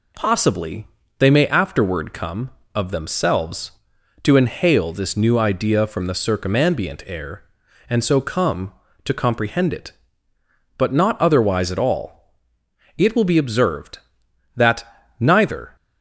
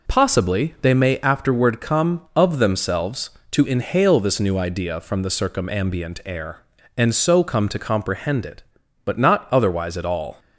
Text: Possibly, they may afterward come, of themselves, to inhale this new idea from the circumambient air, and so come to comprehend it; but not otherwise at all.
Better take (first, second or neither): second